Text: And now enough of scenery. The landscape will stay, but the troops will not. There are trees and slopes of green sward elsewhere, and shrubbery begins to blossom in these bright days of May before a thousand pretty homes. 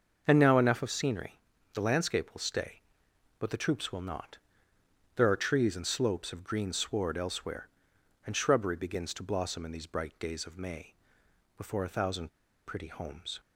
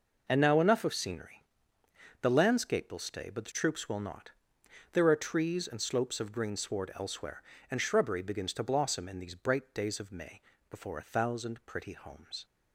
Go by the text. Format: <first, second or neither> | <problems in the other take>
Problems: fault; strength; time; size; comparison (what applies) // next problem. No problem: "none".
second | starts louder than the rest; until 1.2 s; 6.5 dB // pauses between "May" and "before"; noticeable; at 10.9 s; 0.64 s long; slight in the second // pauses between "thousand" and "pretty"; at 12.2 s; 0.38 s long